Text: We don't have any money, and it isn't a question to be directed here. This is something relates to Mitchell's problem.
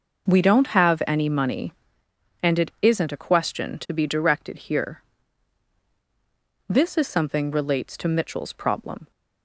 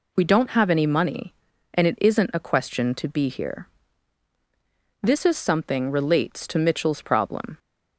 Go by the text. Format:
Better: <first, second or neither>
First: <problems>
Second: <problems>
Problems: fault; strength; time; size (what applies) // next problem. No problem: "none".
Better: first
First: none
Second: skips "directed"; at 3.2 s